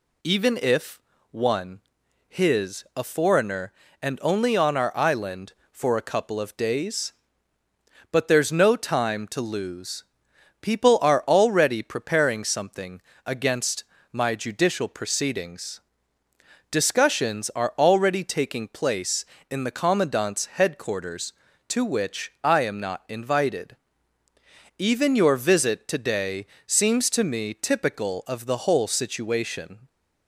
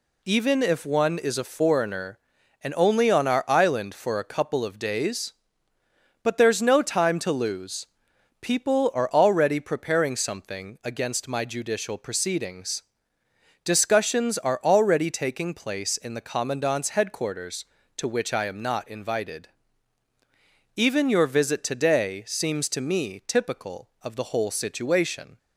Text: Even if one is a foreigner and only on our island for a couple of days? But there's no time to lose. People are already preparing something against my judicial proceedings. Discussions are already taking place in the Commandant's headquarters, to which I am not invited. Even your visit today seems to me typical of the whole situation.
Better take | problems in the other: second | pauses between "if" and "one"; slight; at 0.9 s; 0.32 s long // says "his" for "is"; at 2.3 s // pauses between "something" and "against"; slight; at 13.0 s; 0.24 s long // pauses between "against" and "my"; slight; at 13.8 s; 0.30 s long // pauses between "today" and "seems"; slight; at 26.4 s; 0.22 s long

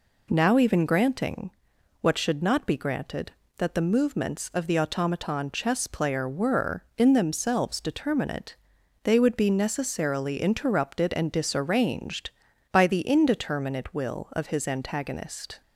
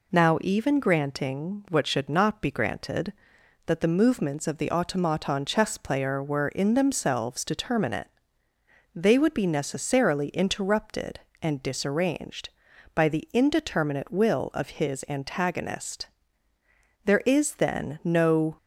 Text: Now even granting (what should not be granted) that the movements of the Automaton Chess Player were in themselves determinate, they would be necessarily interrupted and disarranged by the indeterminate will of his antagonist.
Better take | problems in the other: first | goes on to say "There is then no"; from 17.0 s on; 1.5 s long

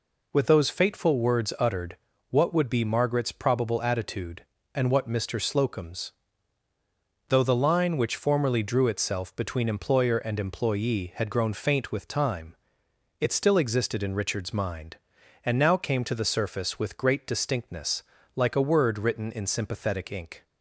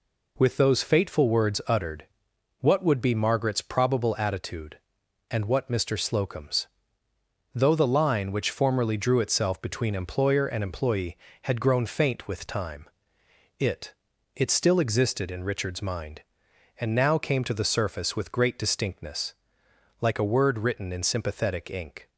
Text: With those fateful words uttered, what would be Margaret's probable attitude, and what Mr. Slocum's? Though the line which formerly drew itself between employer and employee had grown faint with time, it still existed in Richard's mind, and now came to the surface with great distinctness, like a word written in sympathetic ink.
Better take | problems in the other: first | says "it" twice; at 14.3 s

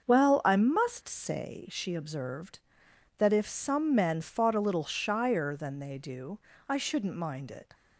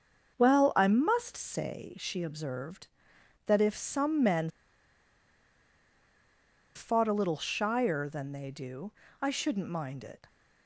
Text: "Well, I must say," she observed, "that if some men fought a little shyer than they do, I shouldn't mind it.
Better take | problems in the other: first | starts louder than the rest; until 1.3 s; 6.5 dB; also in the first // pauses between "men" and "fought"; strong; at 4.4 s; 2.2 s long

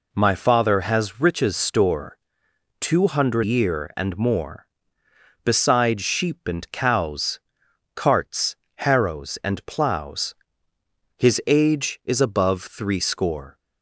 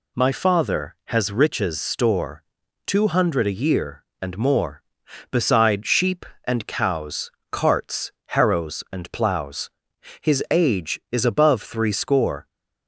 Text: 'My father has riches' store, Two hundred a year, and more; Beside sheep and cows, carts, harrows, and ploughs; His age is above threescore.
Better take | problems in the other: second | skips "a"; at 3.4 s

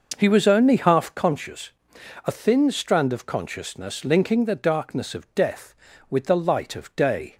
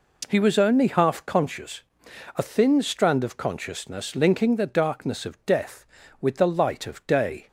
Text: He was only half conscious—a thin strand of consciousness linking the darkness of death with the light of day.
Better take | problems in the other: second | starts louder than the rest; noticeable; until 1.2 s; 6 dB

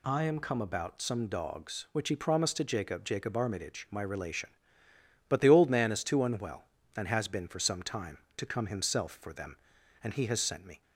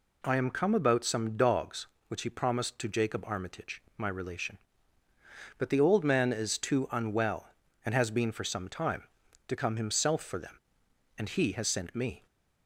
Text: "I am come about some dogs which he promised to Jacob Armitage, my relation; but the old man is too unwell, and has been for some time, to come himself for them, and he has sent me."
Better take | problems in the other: second | says "Jacob" twice; at 3.0 s

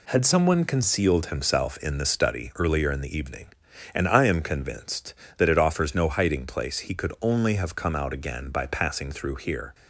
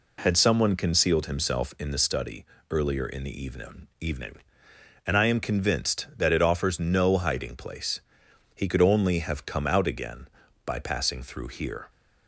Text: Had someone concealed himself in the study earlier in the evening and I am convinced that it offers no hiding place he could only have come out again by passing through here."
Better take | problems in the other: first | pauses between "study" and "earlier"; slight; at 2.4 s; 0.26 s long // says "evening" twice; at 4.0 s // pauses between "place" and "he"; noticeable; at 8.0 s; 0.52 s long

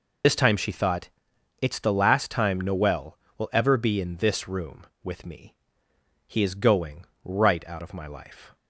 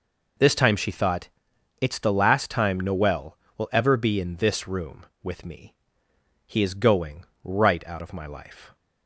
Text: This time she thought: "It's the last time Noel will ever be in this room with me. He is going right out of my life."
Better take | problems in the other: second | loses the start of "This"; at 0.2 s; 55 ms // pauses between "going" and "right"; slight; at 7.0 s; 0.18 s long; slight in the second

